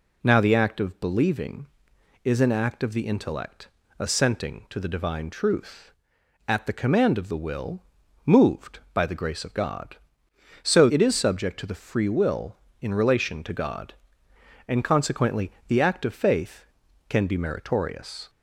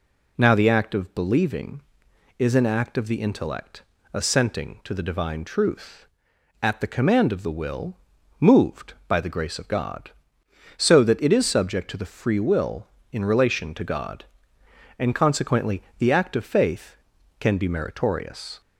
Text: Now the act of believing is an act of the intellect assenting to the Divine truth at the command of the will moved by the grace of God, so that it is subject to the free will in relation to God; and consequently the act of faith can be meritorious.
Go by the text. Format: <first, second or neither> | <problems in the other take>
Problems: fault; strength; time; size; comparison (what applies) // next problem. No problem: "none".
second | pauses between "intellect" and "assenting"; slight; at 3.6 s; 0.30 s long; slight in the second // pauses between "will" and "moved"; at 7.8 s; 0.44 s long; also in the second // skips "that"; at 10.9 s // pauses between "consequently" and "the"; slight; at 15.5 s; 0.16 s long; slight in the second